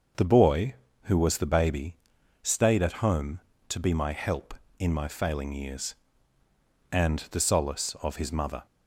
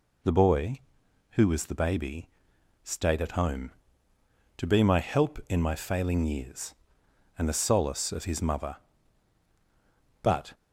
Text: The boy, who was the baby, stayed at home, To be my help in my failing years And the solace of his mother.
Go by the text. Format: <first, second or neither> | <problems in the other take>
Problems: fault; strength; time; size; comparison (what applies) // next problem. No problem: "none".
first | goes on to say "But"; slight; from 10.2 s on; 0.32 s long